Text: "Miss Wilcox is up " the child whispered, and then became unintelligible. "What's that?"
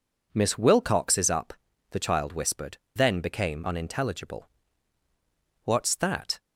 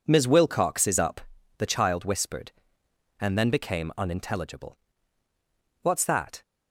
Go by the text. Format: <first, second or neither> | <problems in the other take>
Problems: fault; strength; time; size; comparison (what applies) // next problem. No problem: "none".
second | skips "and"; at 2.8 s